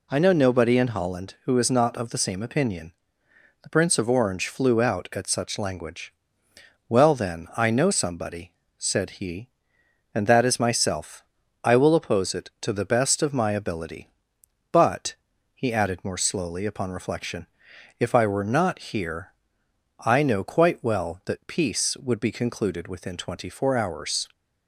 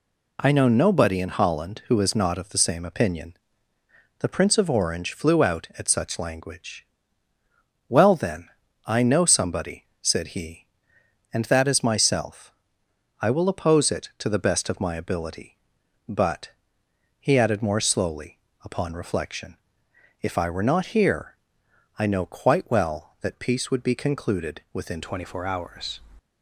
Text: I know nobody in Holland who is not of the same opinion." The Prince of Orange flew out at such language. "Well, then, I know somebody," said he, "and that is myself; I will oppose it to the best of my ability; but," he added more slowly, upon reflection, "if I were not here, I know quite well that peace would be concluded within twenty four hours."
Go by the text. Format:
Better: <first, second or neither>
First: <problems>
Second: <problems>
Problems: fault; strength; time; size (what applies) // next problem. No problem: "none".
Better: first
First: none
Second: changes voice at "twenty"; from 25.0 s on; 1.0 s long